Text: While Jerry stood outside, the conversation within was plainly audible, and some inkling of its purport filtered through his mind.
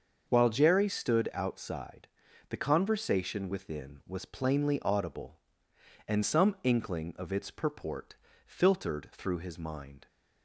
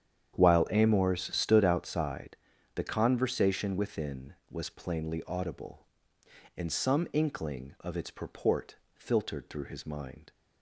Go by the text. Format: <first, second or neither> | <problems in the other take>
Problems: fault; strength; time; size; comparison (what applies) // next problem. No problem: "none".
first | starts louder than the rest; strong; until 1.3 s; 9 dB; also in the first // says "Amors" for "Jerry"; at 0.6 s // pauses between "purport" and "filtered"; slight; at 8.7 s; 0.22 s long; slight in the first